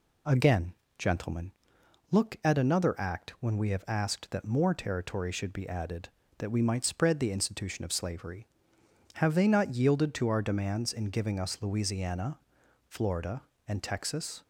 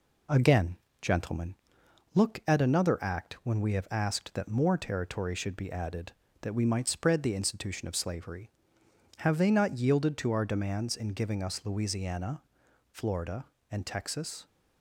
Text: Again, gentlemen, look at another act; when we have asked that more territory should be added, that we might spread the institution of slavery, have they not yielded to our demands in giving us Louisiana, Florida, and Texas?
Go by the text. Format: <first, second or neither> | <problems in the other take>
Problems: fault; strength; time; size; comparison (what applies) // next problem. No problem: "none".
first | gets quieter; slight; throughout; 2 dB